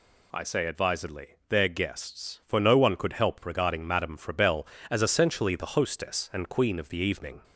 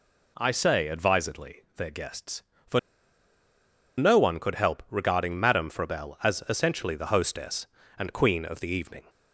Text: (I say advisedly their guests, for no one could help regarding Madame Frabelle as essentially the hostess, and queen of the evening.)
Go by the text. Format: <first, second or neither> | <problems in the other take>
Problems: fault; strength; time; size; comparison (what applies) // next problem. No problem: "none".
first | pauses between "for" and "no"; at 2.7 s; 1.1 s long